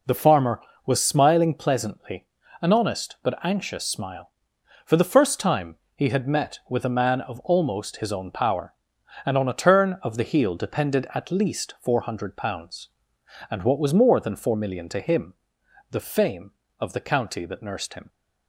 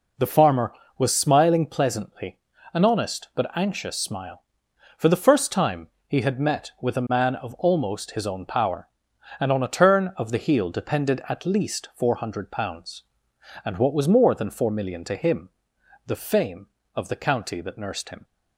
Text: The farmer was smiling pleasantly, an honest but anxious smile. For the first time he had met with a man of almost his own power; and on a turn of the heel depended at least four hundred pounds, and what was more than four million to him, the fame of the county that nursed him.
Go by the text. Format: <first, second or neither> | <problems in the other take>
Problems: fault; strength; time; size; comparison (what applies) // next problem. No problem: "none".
neither | pauses between "time" and "he"; slight; the same in both